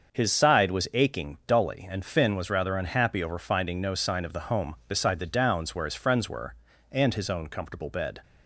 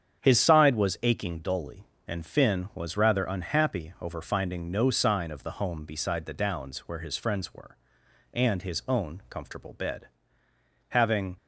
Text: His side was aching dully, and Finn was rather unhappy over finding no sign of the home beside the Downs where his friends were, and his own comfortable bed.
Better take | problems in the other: first | starts louder than the rest; strong; until 1.2 s; 8 dB; also in the first // goes on to say "Having"; slight; from 10.8 s on; 0.48 s long

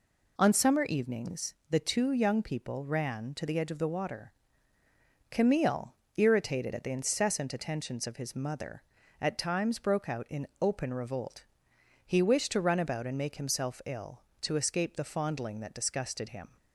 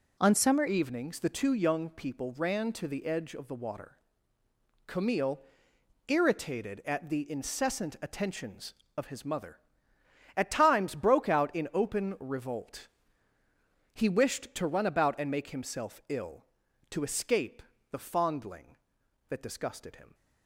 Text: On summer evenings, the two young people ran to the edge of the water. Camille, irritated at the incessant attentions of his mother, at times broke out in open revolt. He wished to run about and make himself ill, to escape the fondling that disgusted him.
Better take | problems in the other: first | changes voice at "evenings"; from 0.6 s on; 19.5 s long // pauses between "escape" and "the"; slight; at 17.6 s; 0.28 s long

